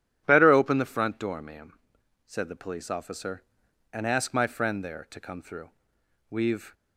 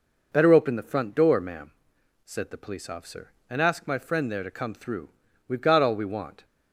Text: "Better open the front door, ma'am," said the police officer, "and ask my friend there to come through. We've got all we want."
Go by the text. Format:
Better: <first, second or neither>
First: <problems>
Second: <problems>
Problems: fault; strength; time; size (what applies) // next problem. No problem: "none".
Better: second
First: stops before "got all we want"; at 6.7 s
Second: none